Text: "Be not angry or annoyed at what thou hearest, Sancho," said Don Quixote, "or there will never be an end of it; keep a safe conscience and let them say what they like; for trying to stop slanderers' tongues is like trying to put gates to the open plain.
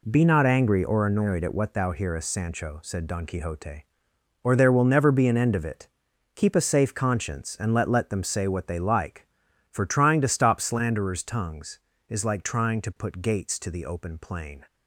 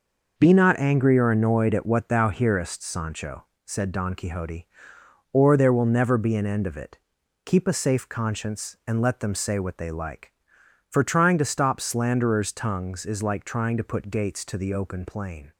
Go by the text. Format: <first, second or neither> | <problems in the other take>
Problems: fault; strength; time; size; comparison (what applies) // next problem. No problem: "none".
second | says "let" twice; at 7.8 s